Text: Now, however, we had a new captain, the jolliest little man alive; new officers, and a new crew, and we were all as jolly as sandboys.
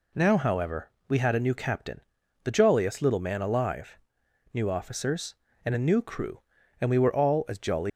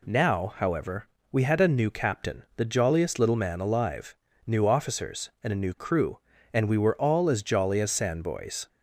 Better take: second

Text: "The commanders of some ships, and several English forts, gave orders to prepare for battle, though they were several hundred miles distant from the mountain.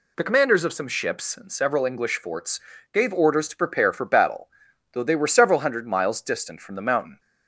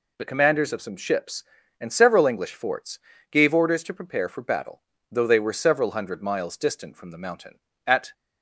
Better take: first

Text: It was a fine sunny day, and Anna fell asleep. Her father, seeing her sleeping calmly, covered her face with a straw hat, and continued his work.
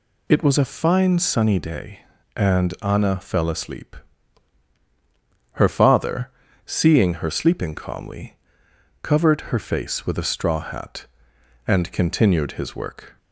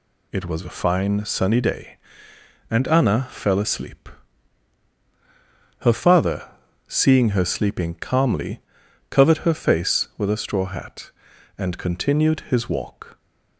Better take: first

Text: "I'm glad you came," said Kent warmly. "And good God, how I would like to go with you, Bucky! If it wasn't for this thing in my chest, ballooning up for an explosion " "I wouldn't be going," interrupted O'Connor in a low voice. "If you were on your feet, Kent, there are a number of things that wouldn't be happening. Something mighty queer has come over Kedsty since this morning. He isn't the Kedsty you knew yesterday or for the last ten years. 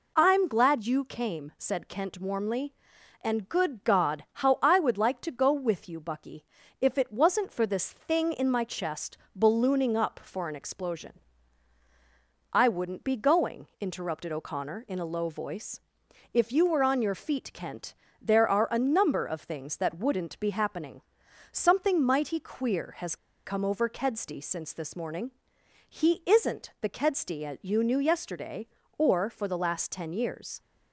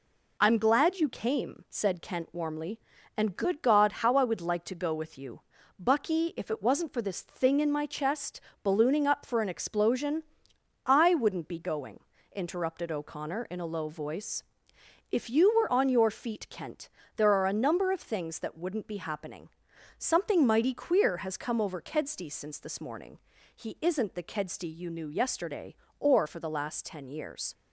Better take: second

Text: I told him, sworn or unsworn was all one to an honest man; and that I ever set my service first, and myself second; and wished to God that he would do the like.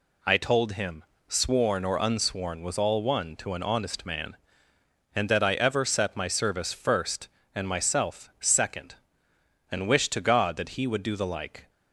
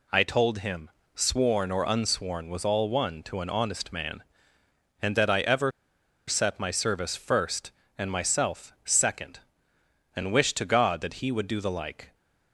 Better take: first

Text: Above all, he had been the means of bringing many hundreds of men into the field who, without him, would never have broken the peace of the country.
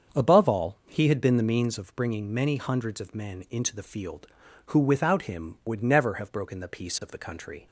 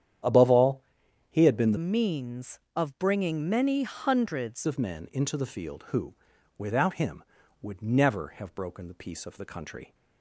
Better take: first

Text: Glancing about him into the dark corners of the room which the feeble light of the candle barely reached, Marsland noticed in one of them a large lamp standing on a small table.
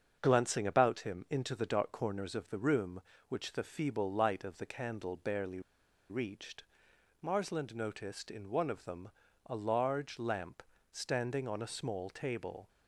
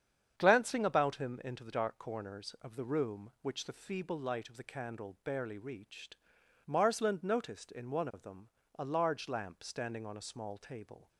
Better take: second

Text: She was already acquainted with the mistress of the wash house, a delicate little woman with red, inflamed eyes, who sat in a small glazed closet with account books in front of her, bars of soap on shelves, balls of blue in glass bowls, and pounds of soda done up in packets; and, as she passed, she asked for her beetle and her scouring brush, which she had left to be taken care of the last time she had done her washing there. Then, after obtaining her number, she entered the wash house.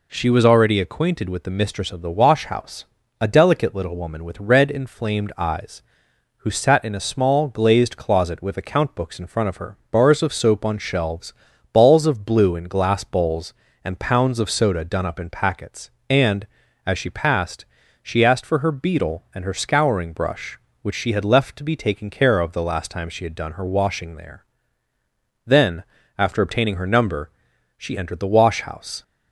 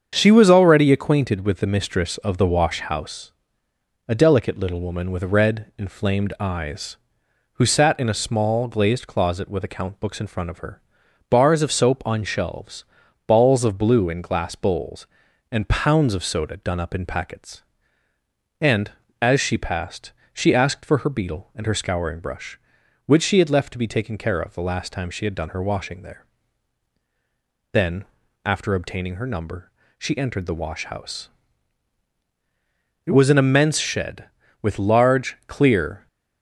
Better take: first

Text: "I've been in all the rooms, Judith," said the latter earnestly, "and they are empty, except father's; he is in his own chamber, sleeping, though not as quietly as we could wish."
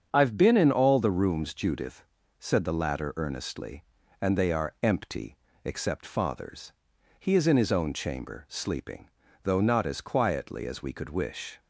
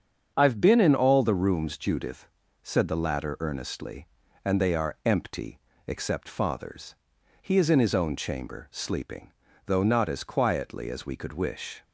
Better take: neither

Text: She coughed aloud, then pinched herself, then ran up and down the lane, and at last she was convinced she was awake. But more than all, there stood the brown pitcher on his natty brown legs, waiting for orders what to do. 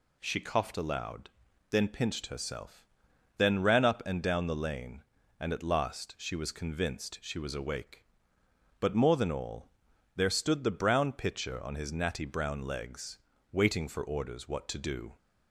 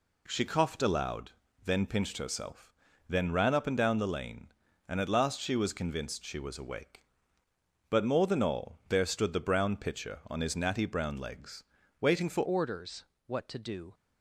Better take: first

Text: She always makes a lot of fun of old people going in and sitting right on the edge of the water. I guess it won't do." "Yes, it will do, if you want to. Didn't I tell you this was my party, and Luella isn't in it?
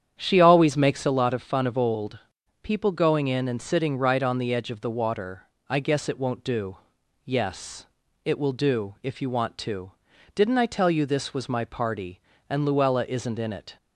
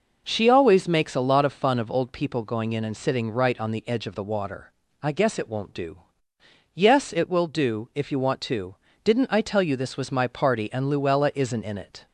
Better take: second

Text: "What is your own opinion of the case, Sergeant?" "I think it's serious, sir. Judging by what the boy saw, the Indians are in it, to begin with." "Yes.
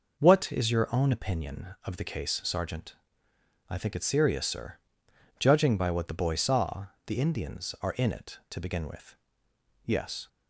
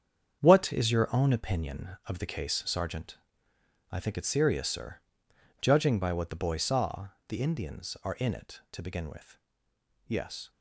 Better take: first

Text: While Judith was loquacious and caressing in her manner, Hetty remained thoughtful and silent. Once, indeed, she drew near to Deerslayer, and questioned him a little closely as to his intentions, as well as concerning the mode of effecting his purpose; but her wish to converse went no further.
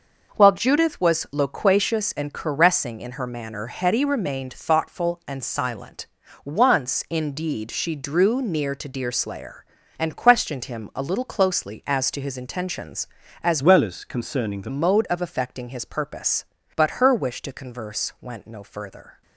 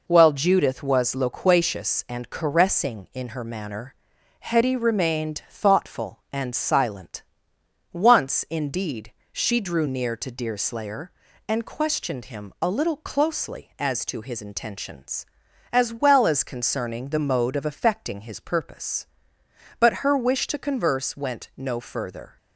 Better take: second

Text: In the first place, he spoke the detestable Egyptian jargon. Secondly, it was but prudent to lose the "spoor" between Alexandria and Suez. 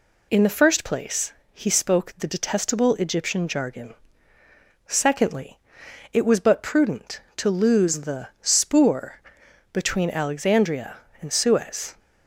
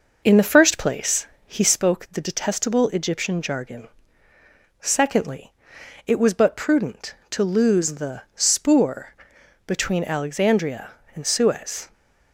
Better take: first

